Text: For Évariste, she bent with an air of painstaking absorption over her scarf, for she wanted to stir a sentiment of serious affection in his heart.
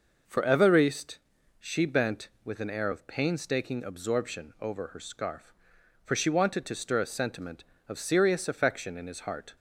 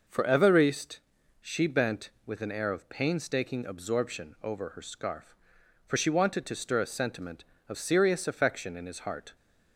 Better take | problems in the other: neither | none

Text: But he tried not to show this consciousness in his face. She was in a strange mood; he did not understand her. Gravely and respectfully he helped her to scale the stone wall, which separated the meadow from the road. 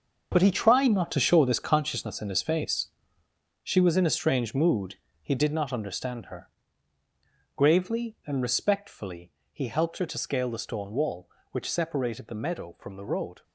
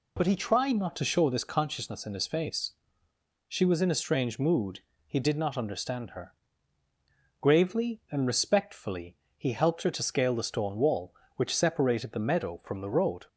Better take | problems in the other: second | gets quieter; strong; throughout; 11.5 dB // pauses between "respectfully" and "he"; slight; at 9.3 s; 0.22 s long; slight in the second

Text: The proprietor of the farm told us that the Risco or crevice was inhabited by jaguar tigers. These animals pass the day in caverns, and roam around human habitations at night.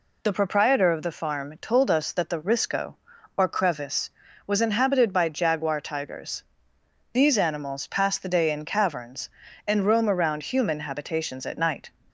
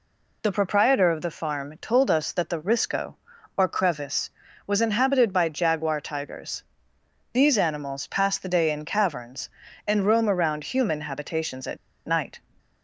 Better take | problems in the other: first | pauses between "at" and "night"; slight; at 11.7 s; 0.28 s long

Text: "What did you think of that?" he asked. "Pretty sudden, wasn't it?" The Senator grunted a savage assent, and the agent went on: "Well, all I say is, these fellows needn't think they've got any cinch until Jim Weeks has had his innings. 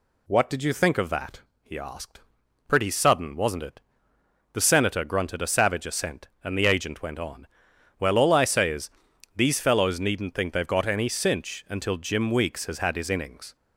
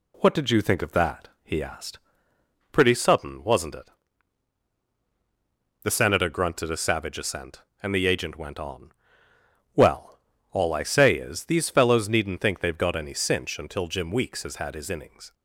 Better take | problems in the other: neither | none

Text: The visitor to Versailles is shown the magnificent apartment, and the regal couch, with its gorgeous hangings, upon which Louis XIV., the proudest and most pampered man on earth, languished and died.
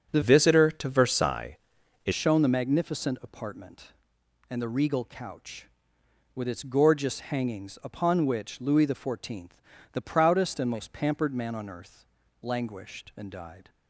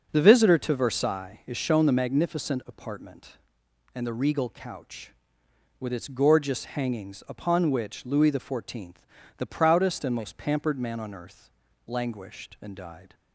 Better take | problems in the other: second | starts louder than the rest; strong; until 1.1 s; 8 dB; also in the second // changes voice from "visitor" to "is"; from 0.2 to 2.1 s; 1.9 s long

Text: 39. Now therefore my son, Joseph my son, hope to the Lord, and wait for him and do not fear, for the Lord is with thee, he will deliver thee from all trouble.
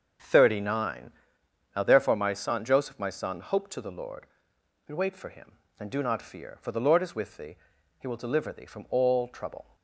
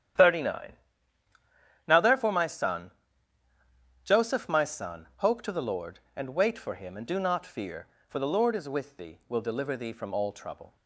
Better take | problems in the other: first | starts louder than the rest; strong; until 2.3 s; 10.5 dB; also in the first // skips "he"; at 9.2 s

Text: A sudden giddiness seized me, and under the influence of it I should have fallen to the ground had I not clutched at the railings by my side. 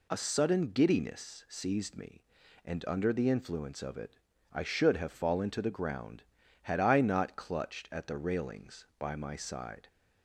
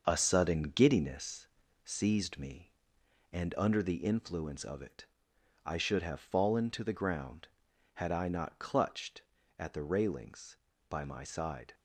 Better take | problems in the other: first | gets quieter; noticeable; throughout; 5.5 dB // pauses between "giddiness" and "seized"; slight; at 1.4 s; 0.36 s long // pauses between "it" and "I"; noticeable; at 5.0 s; 0.58 s long; slight in the first

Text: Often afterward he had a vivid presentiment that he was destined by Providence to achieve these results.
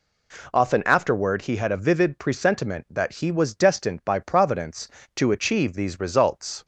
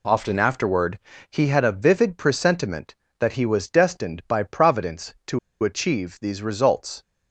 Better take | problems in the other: first | pauses between "afterward" and "he"; slight; at 0.9 s; 0.32 s long // pauses between "to" and "achieve"; slight; at 5.3 s; 0.24 s long

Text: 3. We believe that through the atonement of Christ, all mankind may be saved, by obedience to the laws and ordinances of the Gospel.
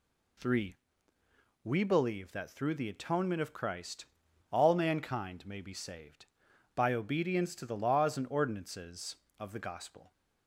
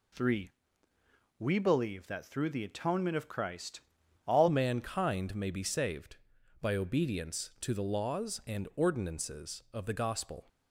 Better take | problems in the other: first | changes voice at "mankind"; from 4.4 s on; 6.0 s long

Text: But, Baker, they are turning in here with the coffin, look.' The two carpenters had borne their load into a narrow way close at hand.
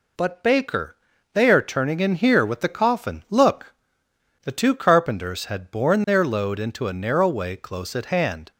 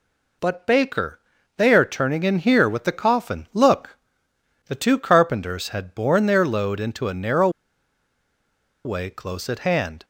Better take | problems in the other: first | pauses between "narrow" and "way"; strong; at 7.4 s; 1.3 s long

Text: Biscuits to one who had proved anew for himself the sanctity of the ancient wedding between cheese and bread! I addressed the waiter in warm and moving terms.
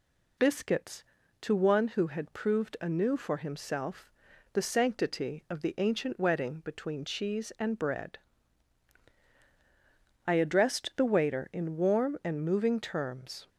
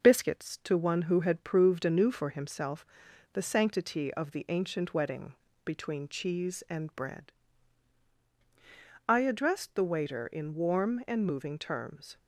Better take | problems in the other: first | gets quieter; slight; throughout; 3.5 dB // pauses between "himself" and "the"; noticeable; at 2.8 s; 0.50 s long; also in the first // pauses between "wedding" and "between"; slight; at 5.3 s; 0.28 s long

